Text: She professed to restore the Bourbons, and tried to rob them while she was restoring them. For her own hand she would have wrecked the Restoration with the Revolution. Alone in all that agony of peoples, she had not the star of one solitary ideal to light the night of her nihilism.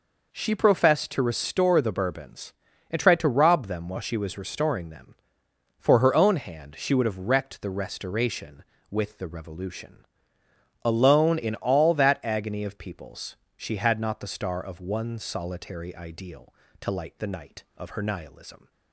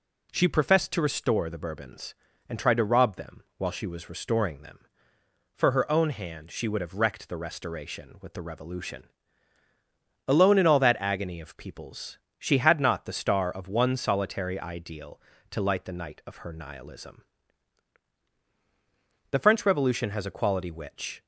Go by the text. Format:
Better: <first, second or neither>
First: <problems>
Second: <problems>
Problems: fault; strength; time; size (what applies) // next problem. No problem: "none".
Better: first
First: none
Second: goes on to say "The French Revolution has a quality which"; strong; from 19.3 s on; 1.9 s long